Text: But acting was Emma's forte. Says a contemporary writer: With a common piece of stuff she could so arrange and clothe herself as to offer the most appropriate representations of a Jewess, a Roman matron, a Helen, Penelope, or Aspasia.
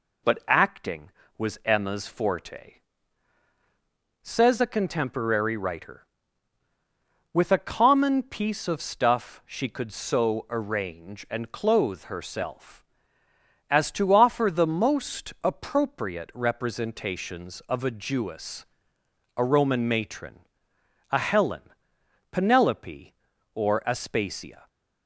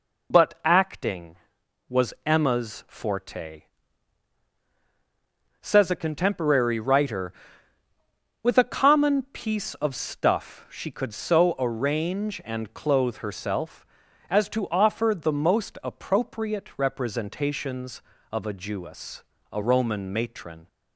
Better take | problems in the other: first | stops before "a Helen Penelope or Aspasia"; at 20.6 s

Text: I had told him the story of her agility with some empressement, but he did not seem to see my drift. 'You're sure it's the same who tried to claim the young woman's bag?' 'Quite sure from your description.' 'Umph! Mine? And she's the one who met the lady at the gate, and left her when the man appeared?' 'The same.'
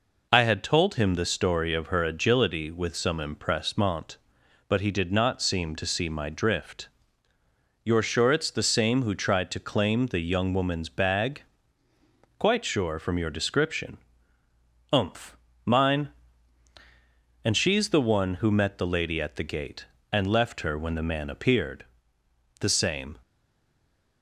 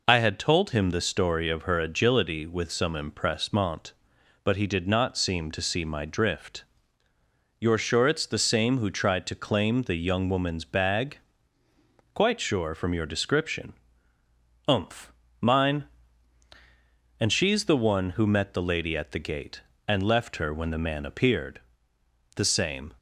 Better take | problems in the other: second | stays silent after the last word; from 23.2 s on; 1.0 s long

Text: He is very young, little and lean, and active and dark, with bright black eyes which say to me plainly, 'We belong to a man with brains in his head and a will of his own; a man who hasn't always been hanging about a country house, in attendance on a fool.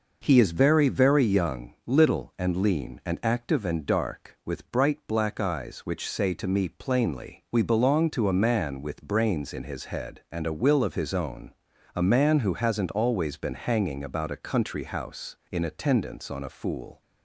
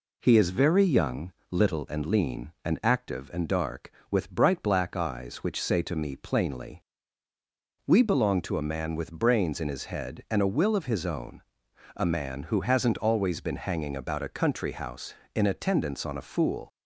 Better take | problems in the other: second | says "very" twice; at 0.8 s

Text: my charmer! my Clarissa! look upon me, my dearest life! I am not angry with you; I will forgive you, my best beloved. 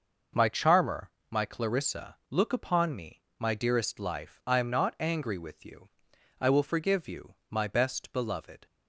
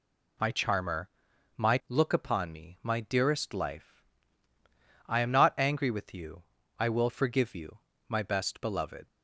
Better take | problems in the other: first | skips "Clarissa"; at 1.8 s

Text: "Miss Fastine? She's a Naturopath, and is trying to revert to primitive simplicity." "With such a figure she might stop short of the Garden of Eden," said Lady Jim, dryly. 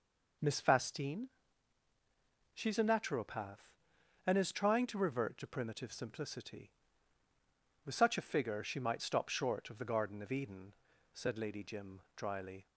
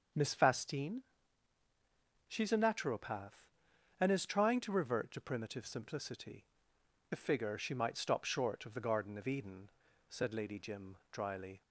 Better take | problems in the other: first | starts louder than the rest; until 2.3 s; 6.5 dB // skips "With such"; at 6.7 s

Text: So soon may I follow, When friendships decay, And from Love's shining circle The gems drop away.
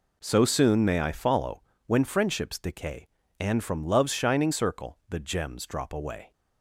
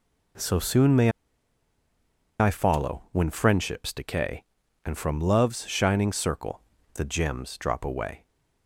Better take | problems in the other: first | pauses between "may" and "I"; strong; at 1.1 s; 1.2 s long // pauses between "circle" and "The"; slight; at 6.6 s; 0.34 s long

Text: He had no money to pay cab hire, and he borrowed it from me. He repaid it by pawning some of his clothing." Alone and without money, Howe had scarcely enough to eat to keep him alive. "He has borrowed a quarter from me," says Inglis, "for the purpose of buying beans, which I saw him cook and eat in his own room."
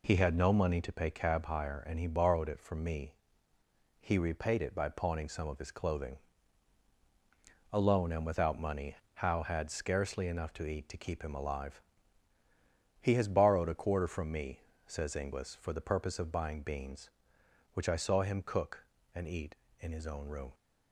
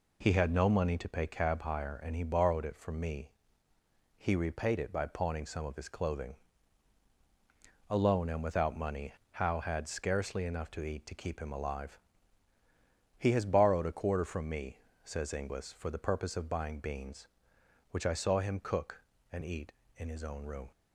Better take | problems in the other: neither | none

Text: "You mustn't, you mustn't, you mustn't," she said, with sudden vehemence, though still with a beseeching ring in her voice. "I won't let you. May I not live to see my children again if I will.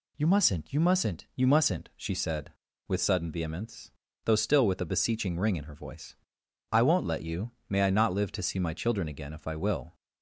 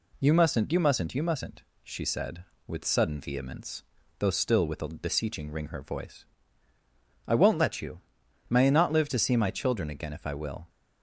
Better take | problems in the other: first | skips "in"; at 5.6 s

